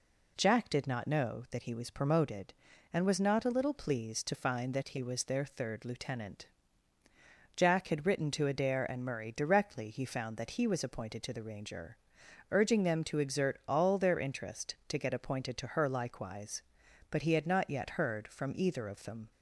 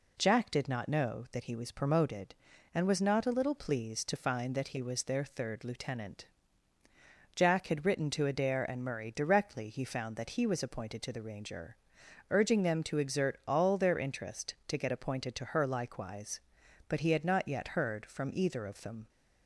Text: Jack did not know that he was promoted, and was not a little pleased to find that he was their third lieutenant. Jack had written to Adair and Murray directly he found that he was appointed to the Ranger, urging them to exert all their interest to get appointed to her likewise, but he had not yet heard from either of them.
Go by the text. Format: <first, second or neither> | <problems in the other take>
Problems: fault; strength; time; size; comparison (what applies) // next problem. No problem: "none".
neither | none